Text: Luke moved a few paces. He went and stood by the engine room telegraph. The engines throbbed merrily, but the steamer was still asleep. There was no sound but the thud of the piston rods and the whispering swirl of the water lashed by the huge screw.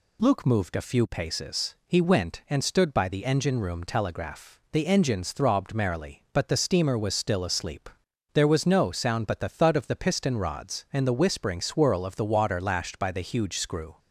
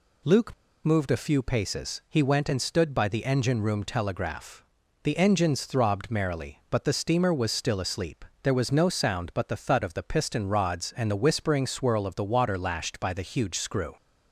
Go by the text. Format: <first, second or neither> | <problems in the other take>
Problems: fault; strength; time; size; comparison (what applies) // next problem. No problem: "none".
first | pauses between "Luke" and "moved"; slight; at 0.5 s; 0.30 s long